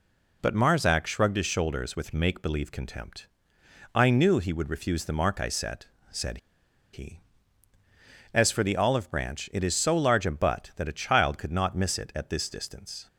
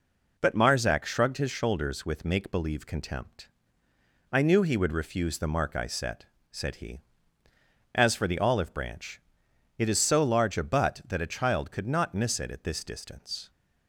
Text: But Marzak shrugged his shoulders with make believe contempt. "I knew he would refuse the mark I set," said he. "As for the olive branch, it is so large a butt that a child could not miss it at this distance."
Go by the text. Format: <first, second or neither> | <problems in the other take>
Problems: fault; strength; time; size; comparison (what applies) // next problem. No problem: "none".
second | pauses between "said" and "he"; noticeable; at 6.3 s; 0.55 s long